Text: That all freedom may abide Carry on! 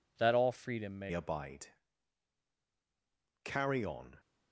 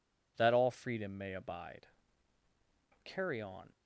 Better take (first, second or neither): second